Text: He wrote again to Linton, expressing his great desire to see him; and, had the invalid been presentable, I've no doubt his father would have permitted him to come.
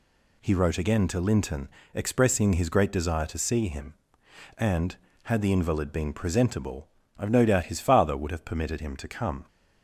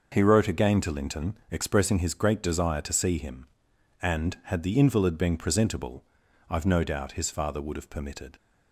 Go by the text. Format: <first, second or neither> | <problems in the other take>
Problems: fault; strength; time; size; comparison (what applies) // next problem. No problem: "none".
first | starts louder than the rest; noticeable; until 1.1 s; 6 dB // stops before "him to come"; at 8.3 s